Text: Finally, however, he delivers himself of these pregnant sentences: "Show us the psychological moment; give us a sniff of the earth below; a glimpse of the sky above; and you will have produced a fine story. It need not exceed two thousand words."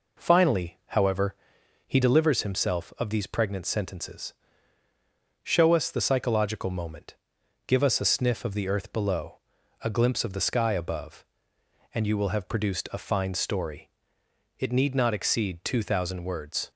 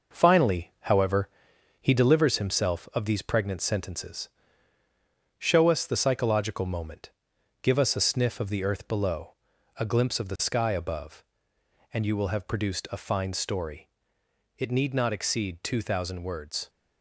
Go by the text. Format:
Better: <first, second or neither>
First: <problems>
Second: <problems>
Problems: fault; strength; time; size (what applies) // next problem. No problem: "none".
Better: first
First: none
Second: gets quieter; noticeable; throughout; 5.5 dB